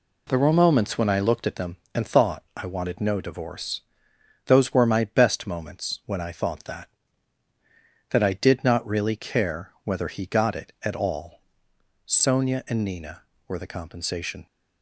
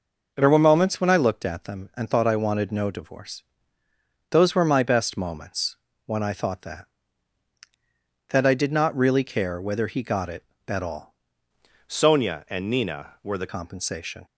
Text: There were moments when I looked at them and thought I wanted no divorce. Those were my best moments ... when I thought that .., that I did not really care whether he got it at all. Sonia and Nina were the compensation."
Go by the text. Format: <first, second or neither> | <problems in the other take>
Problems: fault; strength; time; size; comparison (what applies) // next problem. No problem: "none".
first | changes voice from "Sonia" to "the"; from 11.8 to 13.4 s; 1.6 s long